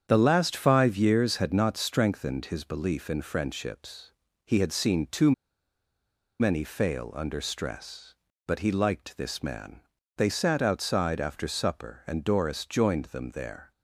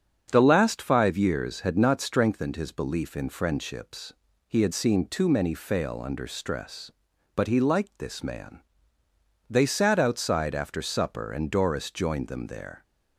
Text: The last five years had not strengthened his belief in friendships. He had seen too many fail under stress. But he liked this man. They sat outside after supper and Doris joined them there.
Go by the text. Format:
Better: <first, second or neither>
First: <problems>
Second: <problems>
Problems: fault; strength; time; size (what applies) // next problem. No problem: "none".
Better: second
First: starts louder than the rest; strong; until 1.1 s; 8 dB // pauses between "too" and "many"; at 5.3 s; 1.0 s long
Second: starts louder than the rest; strong; until 1.3 s; 7.5 dB